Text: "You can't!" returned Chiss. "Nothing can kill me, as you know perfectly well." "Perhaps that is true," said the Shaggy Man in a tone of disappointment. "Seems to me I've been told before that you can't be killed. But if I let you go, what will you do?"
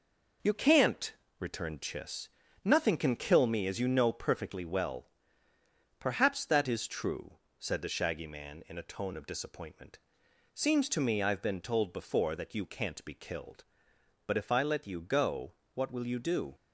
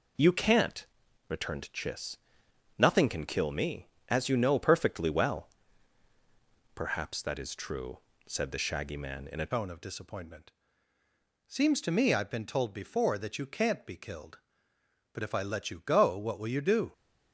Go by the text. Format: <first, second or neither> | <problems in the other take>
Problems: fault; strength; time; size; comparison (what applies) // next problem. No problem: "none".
first | changes voice at "tone"; from 9.5 s on; 7.4 s long